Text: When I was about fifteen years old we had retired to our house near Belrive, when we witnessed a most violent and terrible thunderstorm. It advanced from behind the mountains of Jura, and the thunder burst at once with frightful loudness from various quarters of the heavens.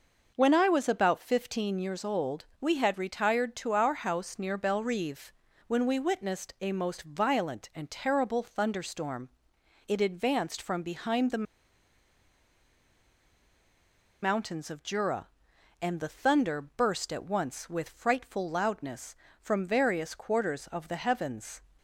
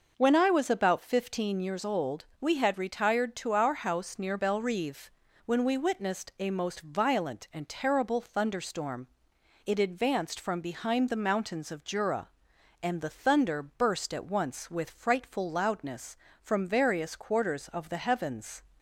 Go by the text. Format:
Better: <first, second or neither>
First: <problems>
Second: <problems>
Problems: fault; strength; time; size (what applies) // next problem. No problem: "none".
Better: second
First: pauses between "the" and "mountains"; strong; at 11.4 s; 2.7 s long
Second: none